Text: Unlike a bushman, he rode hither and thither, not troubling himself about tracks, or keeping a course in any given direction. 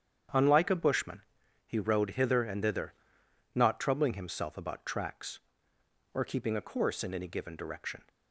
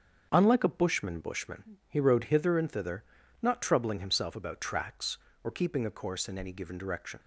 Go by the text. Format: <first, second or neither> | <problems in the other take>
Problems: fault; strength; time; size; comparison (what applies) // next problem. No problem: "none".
first | starts louder than the rest; strong; until 1.3 s; 7 dB; strong in the first // says "bushman" twice; at 1.1 s